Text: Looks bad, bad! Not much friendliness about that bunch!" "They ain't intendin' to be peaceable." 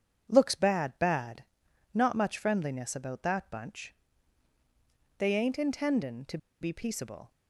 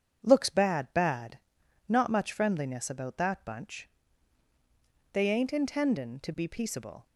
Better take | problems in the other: second | starts louder than the rest; strong; until 1.3 s; 8 dB; strong in the second // pauses between "to" and "be"; slight; at 6.3 s; 0.23 s long

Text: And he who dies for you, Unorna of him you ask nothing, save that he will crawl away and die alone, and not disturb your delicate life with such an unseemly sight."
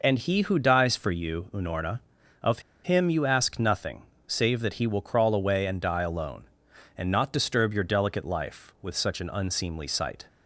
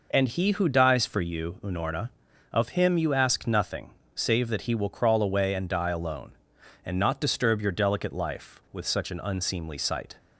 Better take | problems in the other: second | pauses between "of" and "him"; slight; at 2.5 s; 0.24 s long

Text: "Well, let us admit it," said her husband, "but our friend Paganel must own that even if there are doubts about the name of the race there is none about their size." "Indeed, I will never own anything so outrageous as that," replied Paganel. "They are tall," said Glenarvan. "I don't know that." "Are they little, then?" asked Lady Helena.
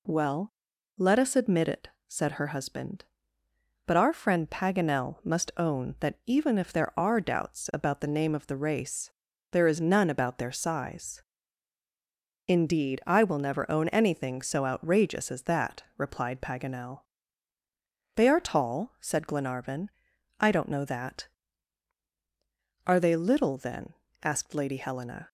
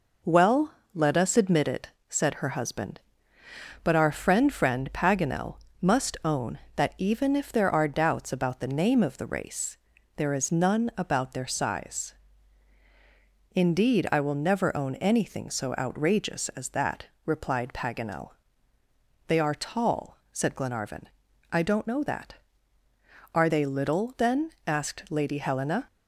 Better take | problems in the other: first | says "friend" twice; at 4.5 s // pauses between "Paganel" and "must"; slight; at 5.5 s; 0.24 s long // pauses between "race" and "there"; at 9.7 s; 0.38 s long; also in the first

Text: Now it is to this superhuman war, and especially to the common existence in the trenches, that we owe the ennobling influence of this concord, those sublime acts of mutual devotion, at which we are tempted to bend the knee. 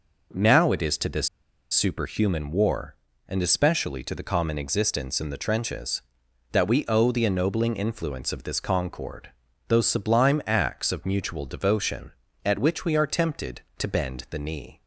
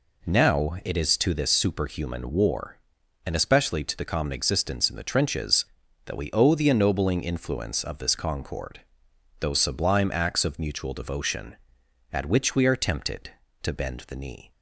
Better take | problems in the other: second | pauses between "this" and "superhuman"; at 1.2 s; 0.43 s long

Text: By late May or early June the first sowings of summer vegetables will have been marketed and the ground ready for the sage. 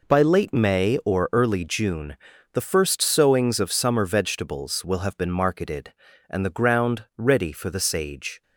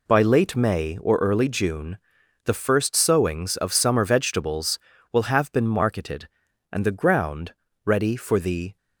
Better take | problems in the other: first | pauses between "June" and "the"; noticeable; at 1.9 s; 0.46 s long; slight in the first // pauses between "ground" and "ready"; slight; at 7.5 s; 0.32 s long // stops before "sage"; at 8.7 s

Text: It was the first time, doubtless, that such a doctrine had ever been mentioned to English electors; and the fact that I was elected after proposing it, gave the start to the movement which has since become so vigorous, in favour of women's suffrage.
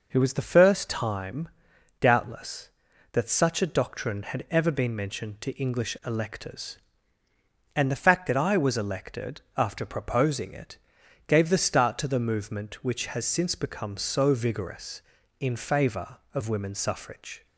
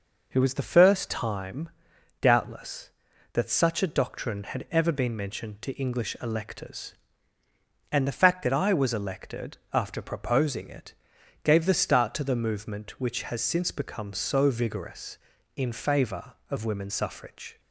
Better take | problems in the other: neither | pauses between "elected" and "after"; slight; the same in both

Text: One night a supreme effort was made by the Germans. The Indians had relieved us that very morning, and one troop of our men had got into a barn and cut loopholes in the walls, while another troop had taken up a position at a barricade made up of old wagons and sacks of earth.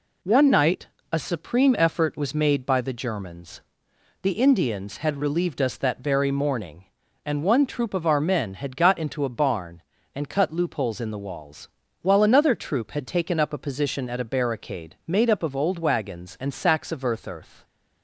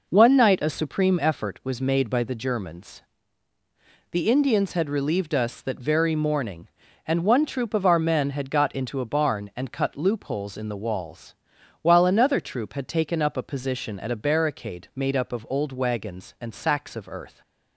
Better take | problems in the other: second | pauses between "night" and "a"; slight; at 0.8 s; 0.26 s long // says "earth" twice; at 17.2 s

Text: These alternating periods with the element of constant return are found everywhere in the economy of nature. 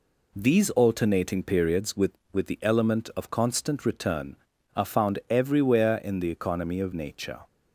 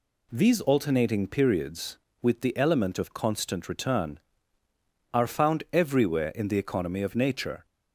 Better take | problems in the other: second | says "with" twice; at 2.3 s

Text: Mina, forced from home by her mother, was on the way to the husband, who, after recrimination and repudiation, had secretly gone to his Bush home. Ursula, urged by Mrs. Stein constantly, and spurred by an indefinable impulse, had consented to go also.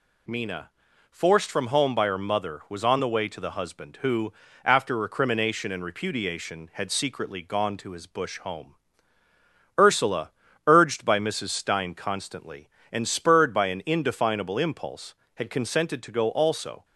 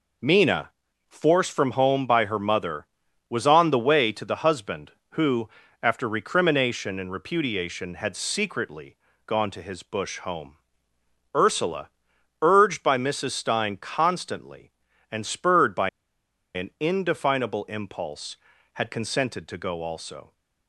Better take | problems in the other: first | pauses between "secretly" and "gone"; slight; at 8.9 s; 0.30 s long // pauses between "by" and "an"; noticeable; at 15.8 s; 0.65 s long

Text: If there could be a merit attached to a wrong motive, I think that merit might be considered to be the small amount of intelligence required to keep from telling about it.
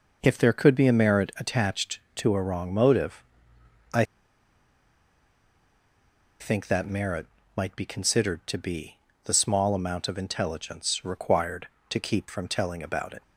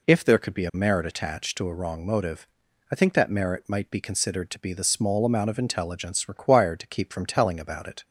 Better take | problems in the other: second | pauses between "I" and "think"; strong; at 4.0 s; 2.3 s long // pauses between "merit" and "might"; slight; at 7.2 s; 0.28 s long // pauses between "be" and "the"; slight; at 8.9 s; 0.28 s long

